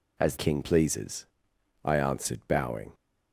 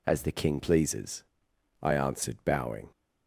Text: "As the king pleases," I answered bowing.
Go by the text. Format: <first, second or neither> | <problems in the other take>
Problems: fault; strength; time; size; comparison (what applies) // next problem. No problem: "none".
second | skips "the"; at 0.3 s